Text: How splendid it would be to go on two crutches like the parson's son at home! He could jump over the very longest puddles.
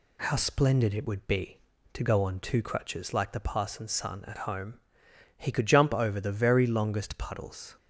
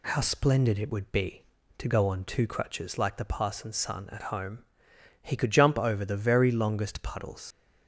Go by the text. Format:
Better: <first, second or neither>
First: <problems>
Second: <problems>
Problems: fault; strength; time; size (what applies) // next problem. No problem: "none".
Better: first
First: none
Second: leaves "puddles" unfinished; at 7.5 s; 105 ms